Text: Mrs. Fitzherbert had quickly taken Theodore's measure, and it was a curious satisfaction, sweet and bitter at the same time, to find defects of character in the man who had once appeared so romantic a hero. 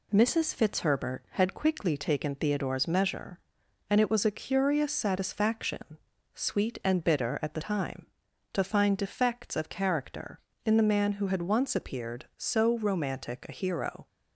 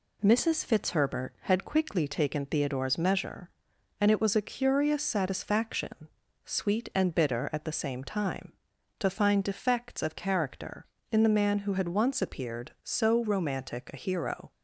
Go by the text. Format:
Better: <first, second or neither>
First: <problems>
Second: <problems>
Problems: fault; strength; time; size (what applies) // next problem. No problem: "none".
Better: second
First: skips "same"; at 7.6 s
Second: none